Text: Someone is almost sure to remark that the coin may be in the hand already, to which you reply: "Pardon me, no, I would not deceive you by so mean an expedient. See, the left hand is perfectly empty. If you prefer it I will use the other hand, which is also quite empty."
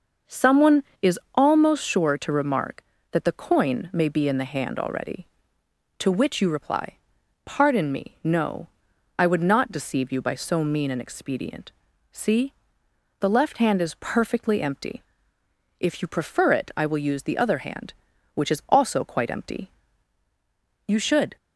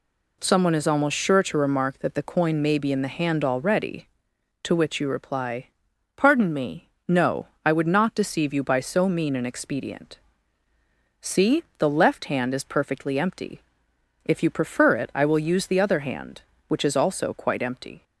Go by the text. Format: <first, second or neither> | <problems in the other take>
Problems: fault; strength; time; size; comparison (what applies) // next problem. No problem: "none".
second | goes on to say "You should"; slight; from 20.8 s on; 0.48 s long